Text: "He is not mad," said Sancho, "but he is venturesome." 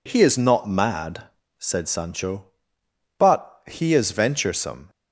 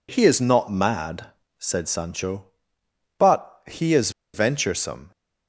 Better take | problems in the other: first | pauses between "is" and "venturesome"; slight; at 4.0 s; 0.24 s long

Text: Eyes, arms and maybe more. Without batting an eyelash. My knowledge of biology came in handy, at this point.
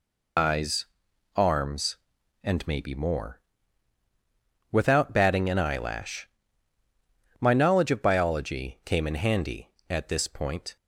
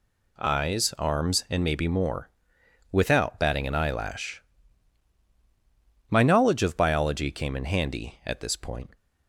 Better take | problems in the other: second | loses the start of "Eyes"; at 0.3 s; 110 ms

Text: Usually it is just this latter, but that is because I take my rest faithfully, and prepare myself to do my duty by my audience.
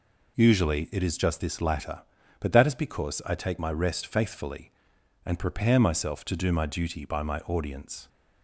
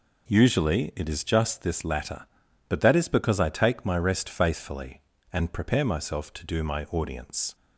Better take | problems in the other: first | skips "duty by my"; at 6.8 s

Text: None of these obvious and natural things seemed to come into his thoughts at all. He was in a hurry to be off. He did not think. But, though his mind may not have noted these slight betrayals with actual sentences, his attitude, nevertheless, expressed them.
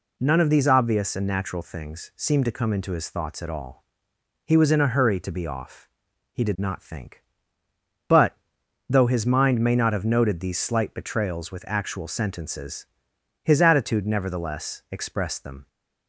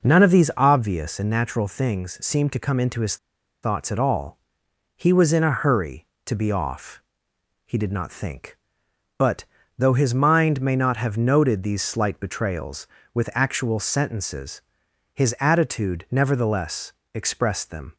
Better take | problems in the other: first | pauses between "his" and "thoughts"; noticeable; at 3.1 s; 0.46 s long

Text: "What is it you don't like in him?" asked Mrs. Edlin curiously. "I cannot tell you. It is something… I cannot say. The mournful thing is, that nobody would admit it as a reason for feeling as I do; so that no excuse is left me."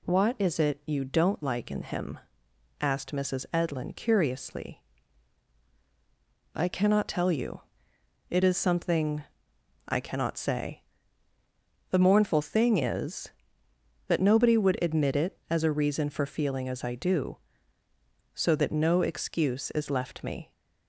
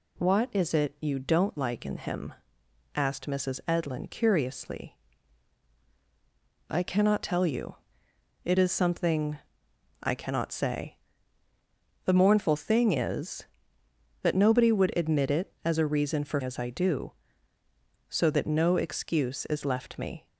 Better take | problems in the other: first | skips "feeling"; at 16.4 s

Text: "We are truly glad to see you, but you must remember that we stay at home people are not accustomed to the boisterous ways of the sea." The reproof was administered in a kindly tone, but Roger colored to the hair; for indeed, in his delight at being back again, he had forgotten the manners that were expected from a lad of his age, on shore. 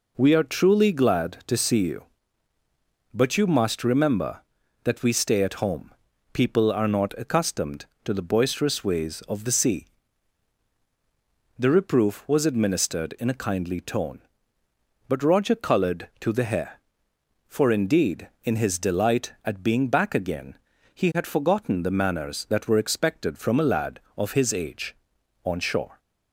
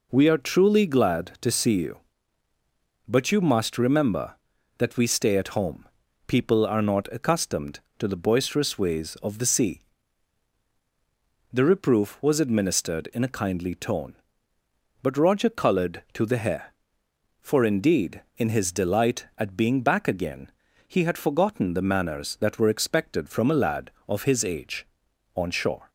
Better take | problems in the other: neither | pauses between "home" and "people"; the same in both

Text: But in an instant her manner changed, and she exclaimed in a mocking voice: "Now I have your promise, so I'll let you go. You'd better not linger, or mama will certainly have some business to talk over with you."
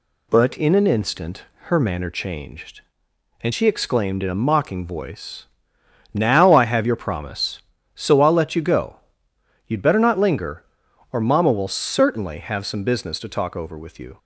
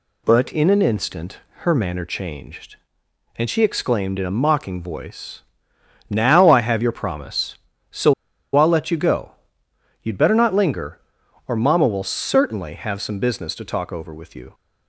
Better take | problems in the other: first | pauses between "instant" and "her"; slight; at 1.3 s; 0.20 s long; slight in the first // pauses between "so" and "I'll"; at 8.1 s; 0.42 s long

